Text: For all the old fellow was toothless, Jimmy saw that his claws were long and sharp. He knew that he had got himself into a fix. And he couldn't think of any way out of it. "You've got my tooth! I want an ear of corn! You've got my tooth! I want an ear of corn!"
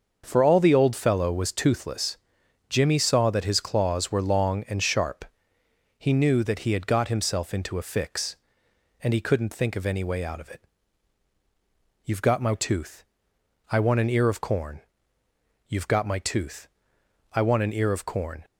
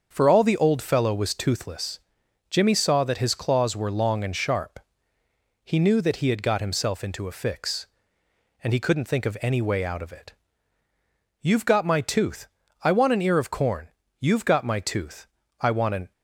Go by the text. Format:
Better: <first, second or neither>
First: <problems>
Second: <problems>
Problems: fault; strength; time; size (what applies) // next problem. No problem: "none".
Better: first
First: starts louder than the rest; until 1.2 s; 6.5 dB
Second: starts louder than the rest; until 1.1 s; 7 dB // stops before "ear of corn"; at 16.1 s